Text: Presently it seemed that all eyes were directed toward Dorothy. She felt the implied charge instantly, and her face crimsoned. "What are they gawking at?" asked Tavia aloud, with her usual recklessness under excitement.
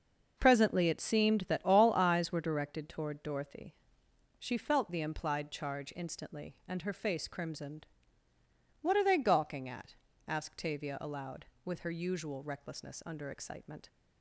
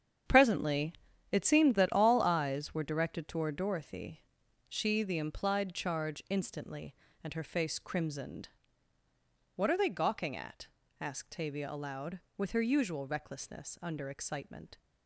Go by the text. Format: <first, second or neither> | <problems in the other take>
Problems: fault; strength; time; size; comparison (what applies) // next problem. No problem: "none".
first | starts louder than the rest; strong; until 1.6 s; 8.5 dB // pauses between "Presently" and "it"; at 0.9 s; 0.38 s long // skips "felt"; at 5.0 s